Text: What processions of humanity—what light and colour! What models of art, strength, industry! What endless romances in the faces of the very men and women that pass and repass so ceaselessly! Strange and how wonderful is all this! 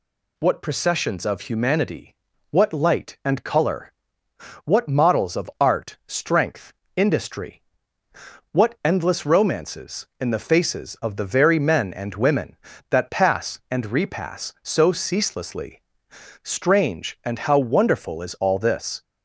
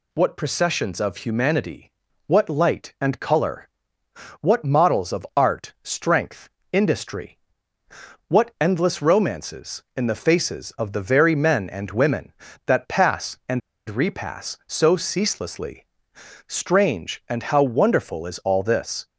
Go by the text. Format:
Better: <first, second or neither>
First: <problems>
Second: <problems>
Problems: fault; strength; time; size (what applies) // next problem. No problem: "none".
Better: first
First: none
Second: pauses between "and" and "repass"; slight; at 13.6 s; 0.29 s long